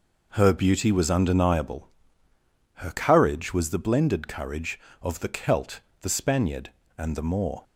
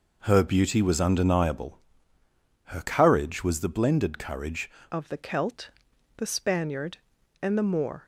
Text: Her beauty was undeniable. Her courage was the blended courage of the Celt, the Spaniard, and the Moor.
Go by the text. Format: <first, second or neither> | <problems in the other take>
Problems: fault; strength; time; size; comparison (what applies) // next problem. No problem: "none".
first | changes voice at "of"; from 4.9 s on; 3.1 s long